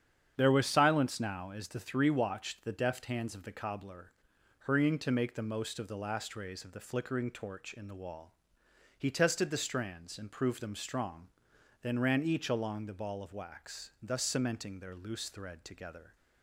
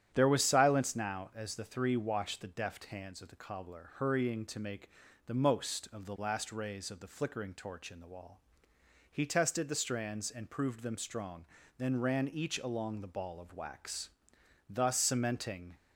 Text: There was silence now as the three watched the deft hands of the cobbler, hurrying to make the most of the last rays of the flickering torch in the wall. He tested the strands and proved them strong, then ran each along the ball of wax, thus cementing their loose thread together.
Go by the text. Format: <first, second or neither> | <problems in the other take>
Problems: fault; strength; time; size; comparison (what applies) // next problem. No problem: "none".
first | starts louder than the rest; strong; until 1.1 s; 9.5 dB; strong in the first // pauses between "make" and "the"; slight; at 4.8 s; 0.36 s long // stops before "their loose thread together"; at 15.7 s